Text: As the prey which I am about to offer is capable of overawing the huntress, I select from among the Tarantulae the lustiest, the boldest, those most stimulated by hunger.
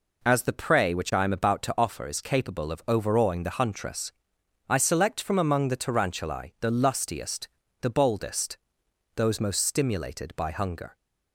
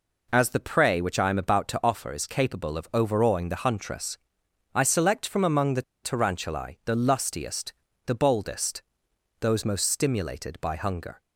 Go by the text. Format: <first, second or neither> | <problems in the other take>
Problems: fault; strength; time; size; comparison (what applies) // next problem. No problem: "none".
first | pauses between "the" and "Tarantulae"; slight; at 5.8 s; 0.21 s long